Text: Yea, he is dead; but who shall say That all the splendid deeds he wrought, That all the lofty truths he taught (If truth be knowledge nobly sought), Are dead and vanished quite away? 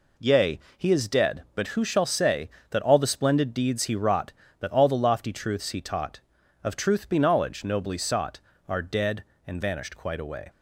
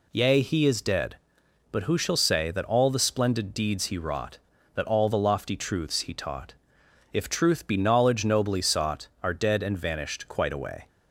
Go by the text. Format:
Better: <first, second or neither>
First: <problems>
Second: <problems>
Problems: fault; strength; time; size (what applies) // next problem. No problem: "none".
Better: second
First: says "Of" for "If"; at 6.6 s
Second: none